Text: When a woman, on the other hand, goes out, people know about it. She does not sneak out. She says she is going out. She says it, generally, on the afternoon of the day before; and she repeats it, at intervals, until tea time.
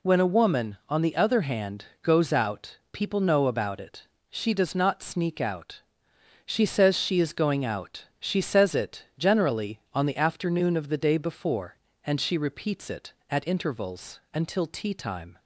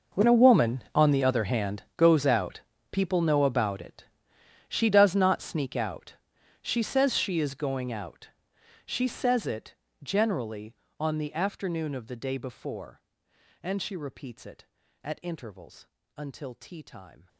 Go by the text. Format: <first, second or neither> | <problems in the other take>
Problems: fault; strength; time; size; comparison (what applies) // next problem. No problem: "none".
first | gets quieter; strong; throughout; 18.5 dB